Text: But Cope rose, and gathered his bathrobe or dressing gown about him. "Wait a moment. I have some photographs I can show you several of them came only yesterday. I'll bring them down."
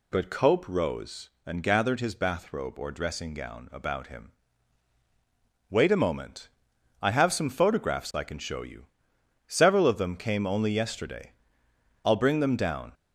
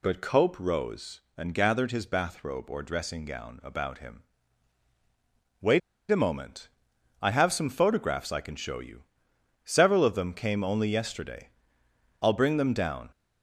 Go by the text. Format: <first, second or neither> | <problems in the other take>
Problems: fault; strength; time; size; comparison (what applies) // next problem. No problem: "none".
first | pauses between "Wait" and "a"; slight; at 5.8 s; 0.30 s long // pauses between "you" and "several"; noticeable; at 9.0 s; 0.60 s long; noticeable in the first